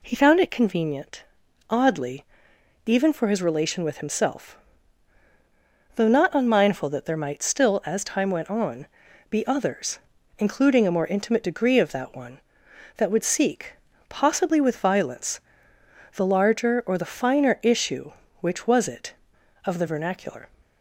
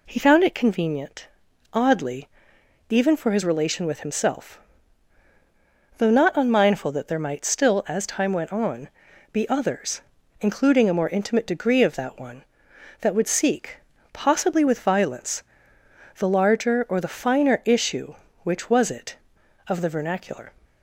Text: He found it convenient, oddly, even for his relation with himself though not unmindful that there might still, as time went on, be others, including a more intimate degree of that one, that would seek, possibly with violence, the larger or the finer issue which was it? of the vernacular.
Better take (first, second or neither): neither